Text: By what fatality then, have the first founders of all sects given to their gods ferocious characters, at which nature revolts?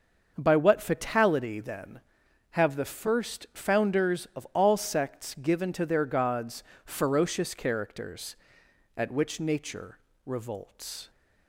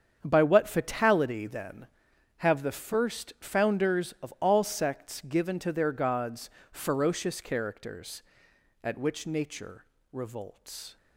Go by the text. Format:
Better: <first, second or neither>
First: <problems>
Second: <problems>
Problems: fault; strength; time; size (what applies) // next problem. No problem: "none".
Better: first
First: starts louder than the rest; until 1.3 s; 6.5 dB // pauses between "gods" and "ferocious"; slight; at 6.6 s; 0.22 s long // pauses between "nature" and "revolts"; slight; at 9.9 s; 0.28 s long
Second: gets quieter; strong; throughout; 12 dB // starts louder than the rest; strong; until 1.2 s; 8 dB // pauses between "gods" and "ferocious"; slight; at 6.5 s; 0.22 s long // pauses between "nature" and "revolts"; slight; at 9.8 s; 0.28 s long